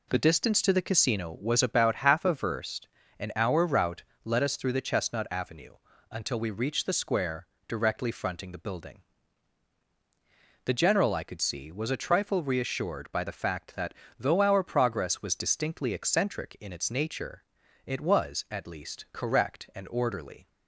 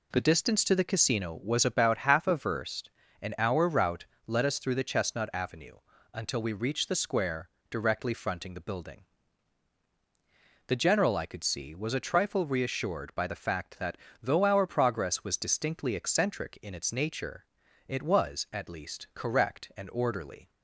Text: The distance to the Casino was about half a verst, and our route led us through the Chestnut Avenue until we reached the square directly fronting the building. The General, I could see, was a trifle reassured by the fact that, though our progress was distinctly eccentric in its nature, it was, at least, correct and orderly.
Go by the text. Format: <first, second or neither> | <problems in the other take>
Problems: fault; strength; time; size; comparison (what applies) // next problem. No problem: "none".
neither | pauses between "route" and "led"; slight; the same in both // pauses between "Avenue" and "until"; slight; the same in both // pauses between "square" and "directly"; slight; the same in both